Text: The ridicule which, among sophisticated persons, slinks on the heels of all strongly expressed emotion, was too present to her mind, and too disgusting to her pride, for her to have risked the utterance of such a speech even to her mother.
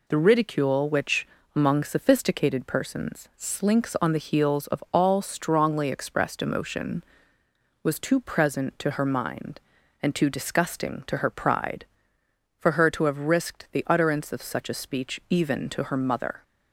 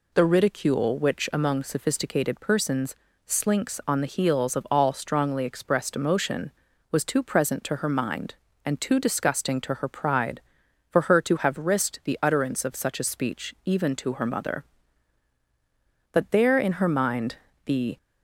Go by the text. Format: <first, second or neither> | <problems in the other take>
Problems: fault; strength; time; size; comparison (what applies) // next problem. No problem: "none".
first | goes on to say "But there in her mind the"; strong; from 16.1 s on; 1.8 s long